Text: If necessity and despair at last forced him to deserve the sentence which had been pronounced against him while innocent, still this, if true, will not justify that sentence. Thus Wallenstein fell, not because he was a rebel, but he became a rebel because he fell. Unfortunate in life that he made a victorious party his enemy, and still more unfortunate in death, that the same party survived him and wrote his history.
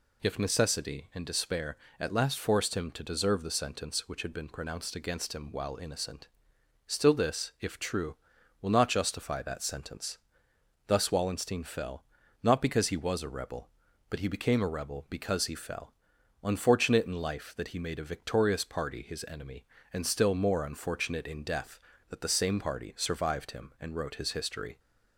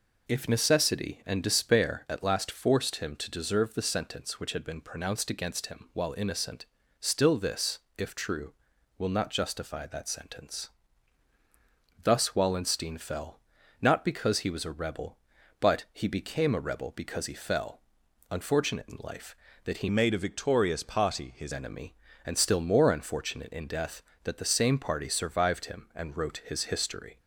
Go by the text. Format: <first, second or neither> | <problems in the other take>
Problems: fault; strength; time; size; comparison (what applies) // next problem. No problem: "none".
first | changes voice from "made" to "his"; from 19.8 to 21.5 s; 1.7 s long